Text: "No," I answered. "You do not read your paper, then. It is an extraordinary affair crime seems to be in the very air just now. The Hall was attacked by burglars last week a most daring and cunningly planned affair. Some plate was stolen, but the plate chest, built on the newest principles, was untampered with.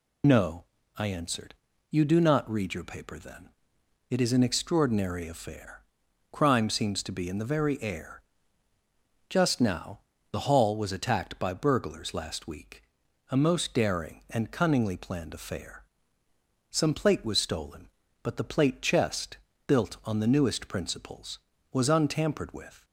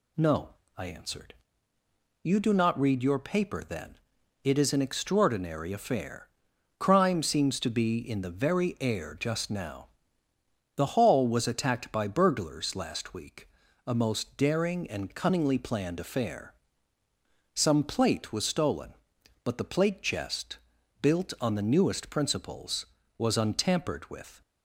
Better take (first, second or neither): second